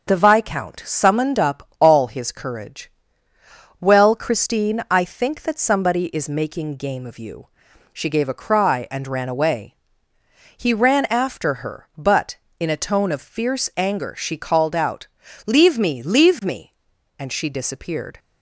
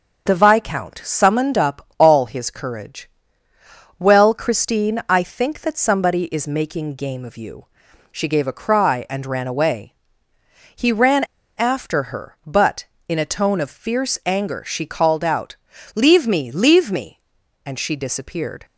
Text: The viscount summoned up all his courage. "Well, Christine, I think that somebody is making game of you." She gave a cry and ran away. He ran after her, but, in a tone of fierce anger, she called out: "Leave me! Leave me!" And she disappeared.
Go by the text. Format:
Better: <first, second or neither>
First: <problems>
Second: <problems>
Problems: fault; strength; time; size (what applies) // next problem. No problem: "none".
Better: first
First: starts louder than the rest; until 1.1 s; 6.5 dB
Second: starts louder than the rest; until 1.3 s; 6.5 dB // pauses between "ran" and "after"; at 11.2 s; 0.36 s long